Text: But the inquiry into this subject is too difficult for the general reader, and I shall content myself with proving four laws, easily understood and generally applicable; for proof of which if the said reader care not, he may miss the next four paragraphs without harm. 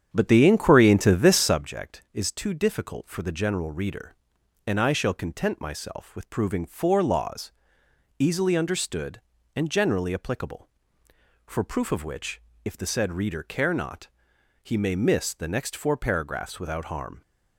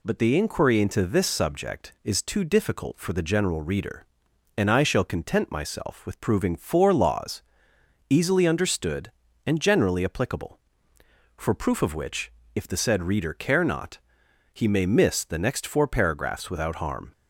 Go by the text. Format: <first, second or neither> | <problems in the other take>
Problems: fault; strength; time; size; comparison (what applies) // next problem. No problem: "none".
second | starts louder than the rest; strong; until 1.6 s; 8.5 dB // pauses between "which" and "if"; slight; at 12.4 s; 0.24 s long; slight in the second